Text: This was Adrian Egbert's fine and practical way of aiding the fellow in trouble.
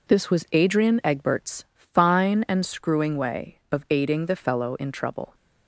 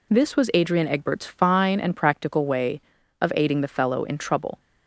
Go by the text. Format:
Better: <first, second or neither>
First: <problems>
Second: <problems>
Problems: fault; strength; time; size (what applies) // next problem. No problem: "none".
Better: second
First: says "screwing" for "practical"; at 2.6 s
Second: none